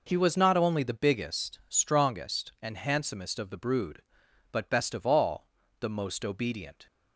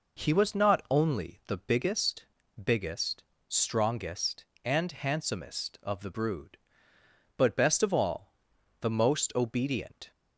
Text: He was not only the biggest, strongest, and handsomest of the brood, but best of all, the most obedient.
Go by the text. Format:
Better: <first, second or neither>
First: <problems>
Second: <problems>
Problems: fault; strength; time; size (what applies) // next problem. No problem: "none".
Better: first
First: none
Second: says "biggest" twice; at 2.6 s